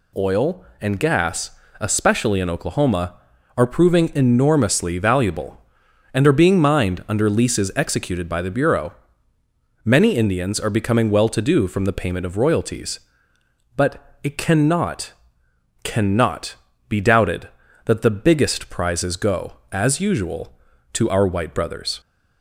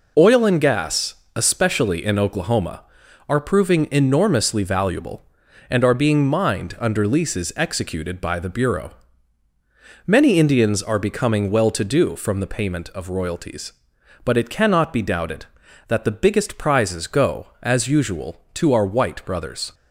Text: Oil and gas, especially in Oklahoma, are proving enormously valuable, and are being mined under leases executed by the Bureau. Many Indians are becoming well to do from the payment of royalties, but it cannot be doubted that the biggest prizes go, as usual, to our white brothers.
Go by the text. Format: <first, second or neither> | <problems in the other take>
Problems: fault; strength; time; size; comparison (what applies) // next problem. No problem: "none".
second | says "cannot" twice; at 15.8 s